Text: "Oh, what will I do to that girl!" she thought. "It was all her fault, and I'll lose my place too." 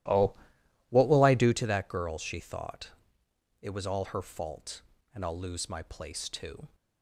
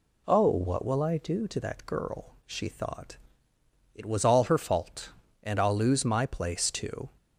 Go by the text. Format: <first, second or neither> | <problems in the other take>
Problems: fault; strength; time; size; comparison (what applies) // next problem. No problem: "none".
second | starts louder than the rest; strong; until 1.6 s; 14 dB